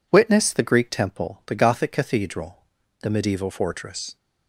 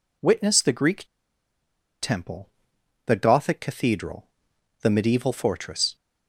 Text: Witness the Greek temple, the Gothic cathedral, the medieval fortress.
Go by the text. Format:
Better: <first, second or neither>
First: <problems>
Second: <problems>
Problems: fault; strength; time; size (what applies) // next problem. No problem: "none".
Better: first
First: none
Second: pauses between "Greek" and "temple"; noticeable; at 1.0 s; 0.97 s long